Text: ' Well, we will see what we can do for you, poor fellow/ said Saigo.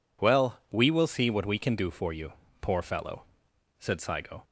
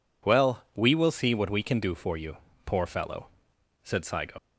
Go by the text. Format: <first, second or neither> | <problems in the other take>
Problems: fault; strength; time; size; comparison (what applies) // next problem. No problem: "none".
first | leaves "Saigo" unfinished; at 4.3 s; 95 ms